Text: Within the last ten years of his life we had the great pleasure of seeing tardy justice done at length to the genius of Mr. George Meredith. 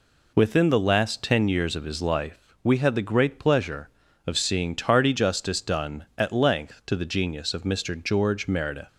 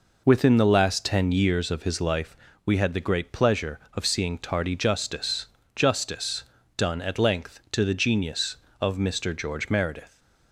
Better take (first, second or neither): first